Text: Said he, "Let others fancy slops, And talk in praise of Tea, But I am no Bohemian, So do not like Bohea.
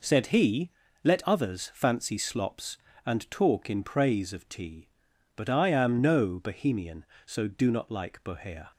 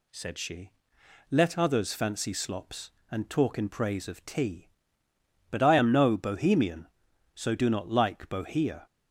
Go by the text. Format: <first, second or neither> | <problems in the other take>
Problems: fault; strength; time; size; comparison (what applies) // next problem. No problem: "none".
first | says "she" for "he"; at 0.3 s